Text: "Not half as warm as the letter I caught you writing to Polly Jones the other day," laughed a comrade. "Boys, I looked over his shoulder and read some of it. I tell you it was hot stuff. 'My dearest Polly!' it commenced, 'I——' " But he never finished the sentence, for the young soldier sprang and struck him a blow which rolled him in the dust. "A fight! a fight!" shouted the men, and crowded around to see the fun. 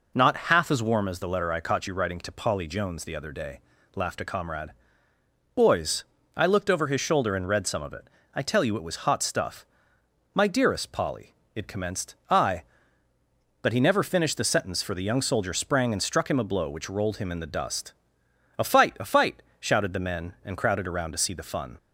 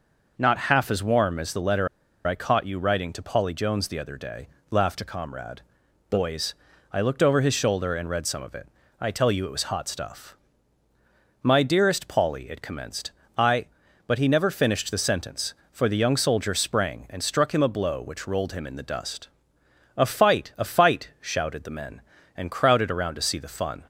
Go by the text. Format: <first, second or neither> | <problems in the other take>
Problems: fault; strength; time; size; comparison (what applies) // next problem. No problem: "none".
first | pauses between "letter" and "I"; at 1.8 s; 0.39 s long